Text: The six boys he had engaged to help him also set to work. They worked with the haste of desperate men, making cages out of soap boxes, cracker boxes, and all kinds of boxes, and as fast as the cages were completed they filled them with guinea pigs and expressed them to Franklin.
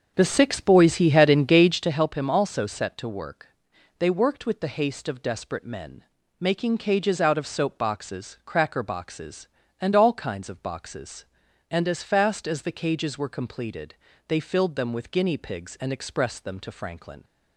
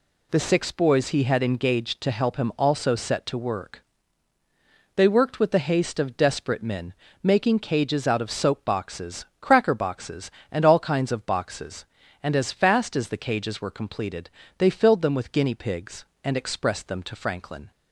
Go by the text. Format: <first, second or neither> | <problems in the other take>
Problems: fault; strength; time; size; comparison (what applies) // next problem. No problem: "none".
second | starts louder than the rest; until 2.0 s; 6.5 dB // pauses between "completed" and "they"; slight; at 13.9 s; 0.36 s long; slight in the second